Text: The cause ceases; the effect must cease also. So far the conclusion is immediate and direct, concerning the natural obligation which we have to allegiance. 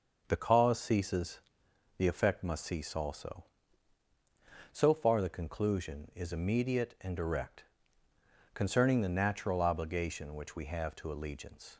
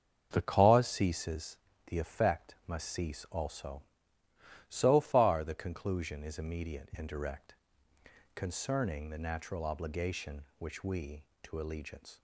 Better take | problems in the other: first | starts louder than the rest; until 1.3 s; 7 dB; also in the first // skips "have"; at 11.3 s

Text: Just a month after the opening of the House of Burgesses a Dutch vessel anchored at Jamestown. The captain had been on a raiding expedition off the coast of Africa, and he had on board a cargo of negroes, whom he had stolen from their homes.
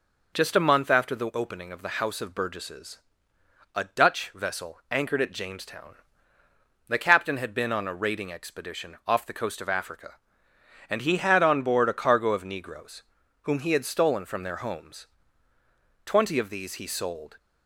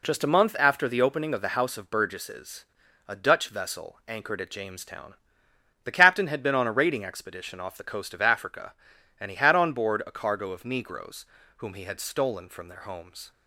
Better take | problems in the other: second | pauses between "Burgesses" and "a"; noticeable; at 2.9 s; 0.76 s long; also in the second // goes on to say "Twenty of these he sold"; noticeable; from 16.0 s on; 1.3 s long

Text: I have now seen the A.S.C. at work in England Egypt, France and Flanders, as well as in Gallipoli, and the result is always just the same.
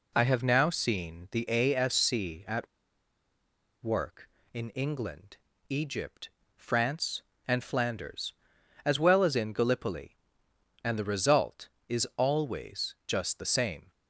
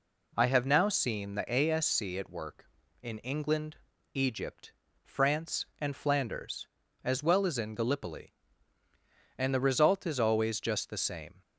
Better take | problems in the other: second | pauses between "at" and "work"; at 2.6 s; 1.1 s long // pauses between "England" and "Egypt"; slight; at 5.3 s; 0.32 s long; also in the second

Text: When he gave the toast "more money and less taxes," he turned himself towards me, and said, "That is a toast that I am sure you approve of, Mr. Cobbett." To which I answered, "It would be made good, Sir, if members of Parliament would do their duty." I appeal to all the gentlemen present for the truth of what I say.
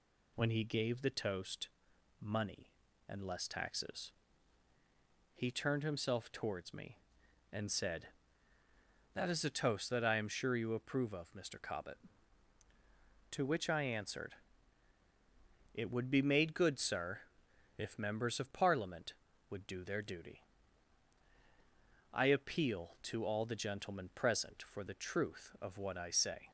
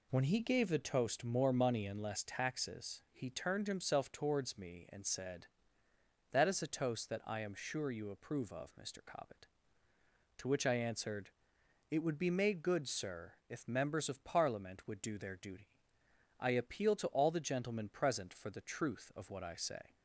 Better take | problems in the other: second | skips "more"; at 1.9 s

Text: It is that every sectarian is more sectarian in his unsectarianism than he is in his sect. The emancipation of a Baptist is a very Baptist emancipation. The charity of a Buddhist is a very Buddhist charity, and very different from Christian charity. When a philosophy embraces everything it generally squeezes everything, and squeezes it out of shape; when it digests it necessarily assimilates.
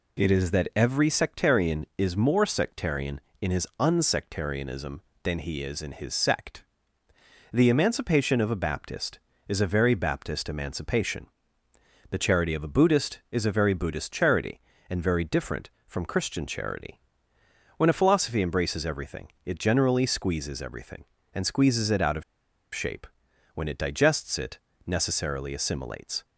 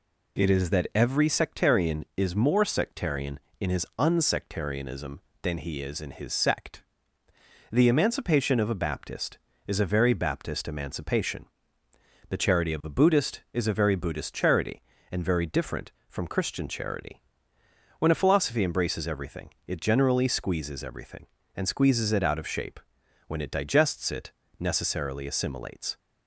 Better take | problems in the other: second | pauses between "everything" and "it"; slight; at 19.2 s; 0.16 s long; slight in the second // pauses between "of" and "shape"; noticeable; at 22.2 s; 0.51 s long // pauses between "it" and "necessarily"; slight; at 24.5 s; 0.26 s long; slight in the second

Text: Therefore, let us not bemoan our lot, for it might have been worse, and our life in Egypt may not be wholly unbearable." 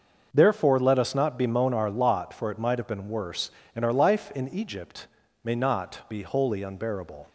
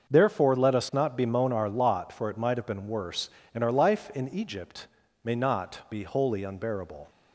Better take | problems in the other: neither | starts louder than the rest; noticeable; the same in both // pauses between "Egypt" and "may"; slight; the same in both

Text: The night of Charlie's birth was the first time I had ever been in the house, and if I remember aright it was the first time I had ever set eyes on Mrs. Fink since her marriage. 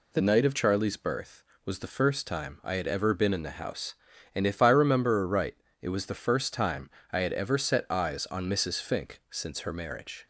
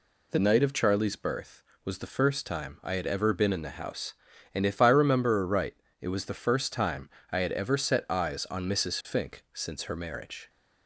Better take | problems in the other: neither | pauses between "aright" and "it"; slight; the same in both // pauses between "time" and "I"; slight; the same in both

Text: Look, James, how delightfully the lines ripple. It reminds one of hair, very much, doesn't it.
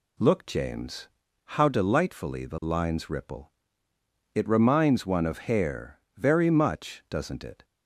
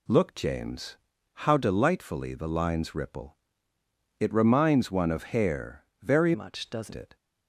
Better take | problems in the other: first | changes voice from "much" to "doesn't"; from 6.3 to 6.9 s; 0.6 s long

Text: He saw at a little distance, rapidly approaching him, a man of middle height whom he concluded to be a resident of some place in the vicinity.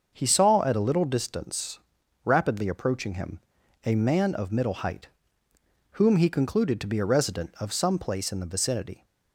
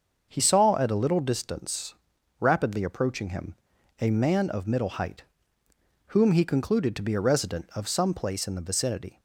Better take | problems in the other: neither | starts louder than the rest; the same in both // pauses between "height" and "whom"; noticeable; the same in both

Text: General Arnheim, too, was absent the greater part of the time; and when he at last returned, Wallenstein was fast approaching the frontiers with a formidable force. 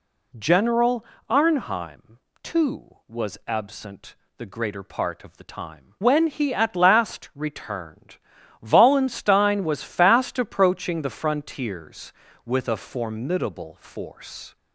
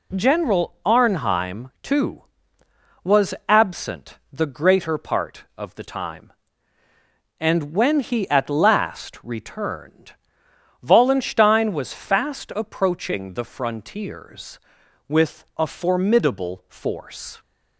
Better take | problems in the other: second | pauses between "General" and "Arnheim"; slight; at 1.0 s; 0.24 s long // pauses between "absent" and "the"; slight; at 4.1 s; 0.22 s long // skips "and"; at 5.9 s

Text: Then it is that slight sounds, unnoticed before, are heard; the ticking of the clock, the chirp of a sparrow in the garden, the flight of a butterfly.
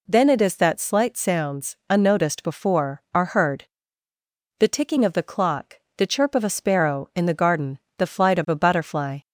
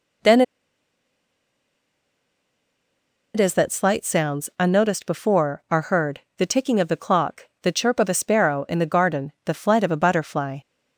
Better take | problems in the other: first | pauses between "Then" and "it"; strong; at 0.4 s; 2.9 s long

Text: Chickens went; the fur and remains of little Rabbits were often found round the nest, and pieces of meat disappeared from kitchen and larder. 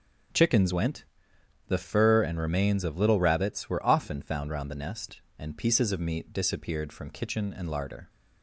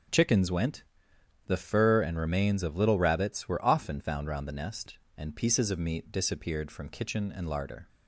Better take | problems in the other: neither | starts louder than the rest; the same in both

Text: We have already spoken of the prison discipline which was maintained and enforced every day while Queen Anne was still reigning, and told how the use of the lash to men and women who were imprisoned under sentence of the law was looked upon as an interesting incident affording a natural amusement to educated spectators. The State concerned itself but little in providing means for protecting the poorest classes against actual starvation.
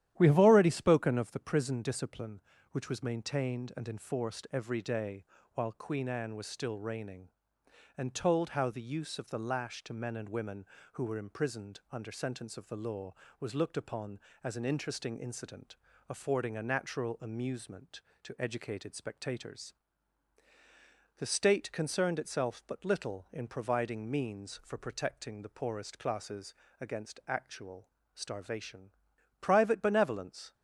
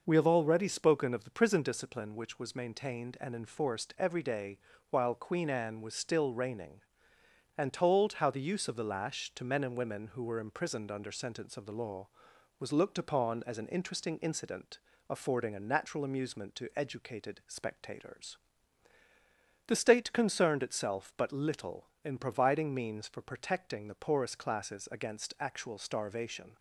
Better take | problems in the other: second | starts louder than the rest; strong; until 1.1 s; 11.5 dB // pauses between "day" and "while"; slight; at 5.2 s; 0.30 s long; slight in the second // pauses between "incident" and "affording"; slight; at 15.7 s; 0.34 s long; slight in the second // pauses between "classes" and "against"; slight; at 26.5 s; 0.26 s long // pauses between "actual" and "starvation"; slight; at 27.8 s; 0.26 s long // goes on to say "Private benevolence"; noticeable; from 29.4 s on; 1.1 s long

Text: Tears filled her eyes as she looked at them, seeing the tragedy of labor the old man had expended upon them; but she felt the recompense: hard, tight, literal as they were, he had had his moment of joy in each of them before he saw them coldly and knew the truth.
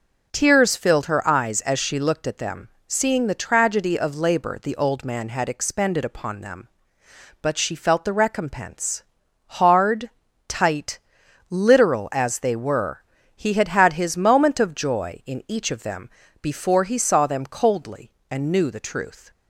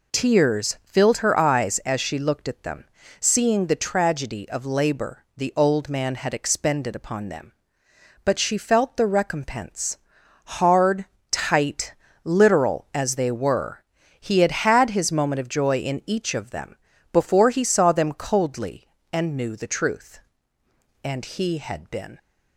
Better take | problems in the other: first | pauses between "them" and "before"; slight; at 16.7 s; 0.36 s long; slight in the first // goes on to say "And he had been"; noticeable; from 21.0 s on; 1.1 s long

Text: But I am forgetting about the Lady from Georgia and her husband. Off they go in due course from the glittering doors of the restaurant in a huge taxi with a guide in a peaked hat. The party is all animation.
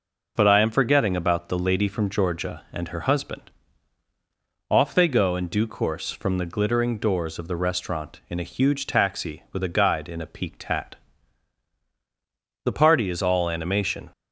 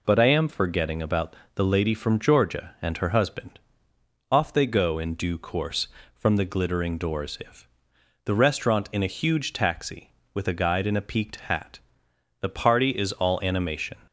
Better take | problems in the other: first | pauses between "about" and "the"; slight; at 1.3 s; 0.22 s long // says "if" for "of"; at 7.3 s

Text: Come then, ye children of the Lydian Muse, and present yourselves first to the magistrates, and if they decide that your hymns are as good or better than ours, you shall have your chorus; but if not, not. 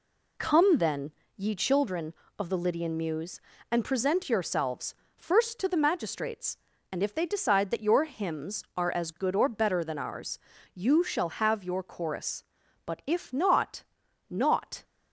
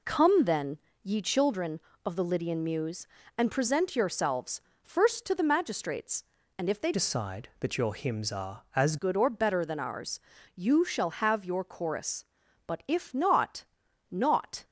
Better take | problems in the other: first | pauses between "yourselves" and "first"; slight; at 4.6 s; 0.22 s long; slight in the first // changes voice from "decide" to "as"; from 6.9 to 8.9 s; 2.0 s long

